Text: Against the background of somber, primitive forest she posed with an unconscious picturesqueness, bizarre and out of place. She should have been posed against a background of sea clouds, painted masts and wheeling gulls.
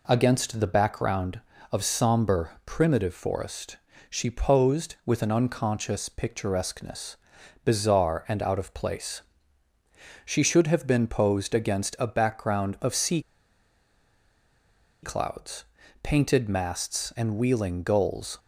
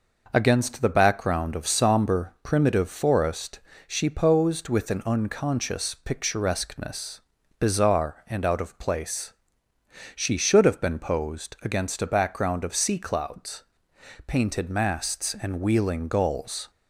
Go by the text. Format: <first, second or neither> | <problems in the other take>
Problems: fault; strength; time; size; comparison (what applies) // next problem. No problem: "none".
second | pauses between "forest" and "she"; slight; at 3.7 s; 0.30 s long; slight in the second // pauses between "sea" and "clouds"; strong; at 13.2 s; 1.8 s long